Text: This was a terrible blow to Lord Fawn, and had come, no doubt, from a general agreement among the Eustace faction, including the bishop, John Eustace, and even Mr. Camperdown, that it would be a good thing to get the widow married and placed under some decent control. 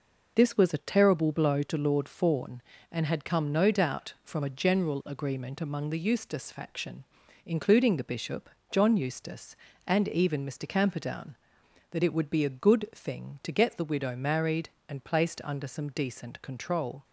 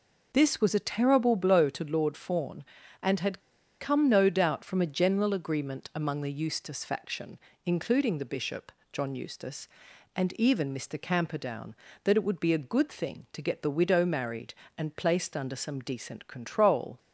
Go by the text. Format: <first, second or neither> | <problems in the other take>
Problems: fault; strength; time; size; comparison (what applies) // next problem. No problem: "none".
first | pauses between "had" and "come"; at 3.4 s; 0.40 s long